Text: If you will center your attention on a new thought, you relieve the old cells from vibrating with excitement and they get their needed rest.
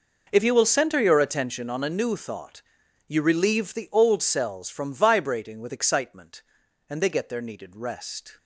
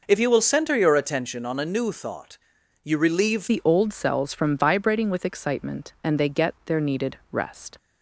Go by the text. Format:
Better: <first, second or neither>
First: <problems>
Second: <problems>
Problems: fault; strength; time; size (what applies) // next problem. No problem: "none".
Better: first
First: none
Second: changes voice at "the"; from 3.4 s on; 4.3 s long